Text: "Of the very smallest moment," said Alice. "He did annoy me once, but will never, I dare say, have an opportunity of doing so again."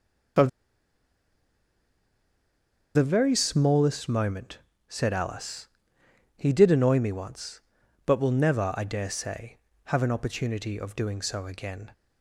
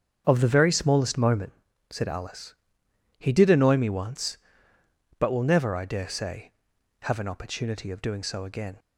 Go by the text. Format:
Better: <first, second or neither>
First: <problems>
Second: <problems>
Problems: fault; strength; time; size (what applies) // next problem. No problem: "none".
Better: second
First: starts louder than the rest; until 3.8 s; 6.5 dB // pauses between "Of" and "the"; strong; at 0.4 s; 2.4 s long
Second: starts louder than the rest; strong; until 1.2 s; 7.5 dB